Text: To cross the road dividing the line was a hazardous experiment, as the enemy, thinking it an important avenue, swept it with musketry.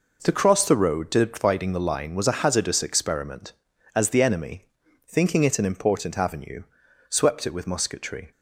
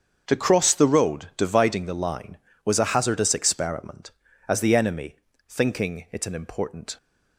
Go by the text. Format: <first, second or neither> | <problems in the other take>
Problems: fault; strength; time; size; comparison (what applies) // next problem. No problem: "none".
first | starts louder than the rest; until 1.2 s; 7 dB // stops before "avenue swept it with musketry"; at 6.9 s